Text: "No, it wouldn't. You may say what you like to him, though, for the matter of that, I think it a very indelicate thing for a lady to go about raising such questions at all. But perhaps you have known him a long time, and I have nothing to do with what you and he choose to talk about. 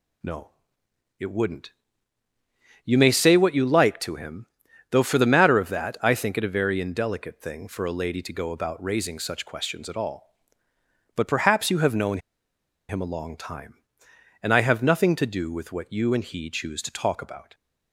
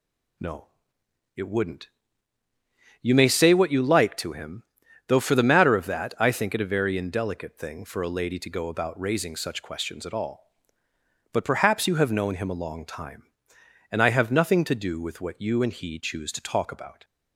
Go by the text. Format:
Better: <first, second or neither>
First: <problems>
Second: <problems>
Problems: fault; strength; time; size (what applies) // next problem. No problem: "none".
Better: second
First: pauses between "known" and "him"; noticeable; at 12.1 s; 0.71 s long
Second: none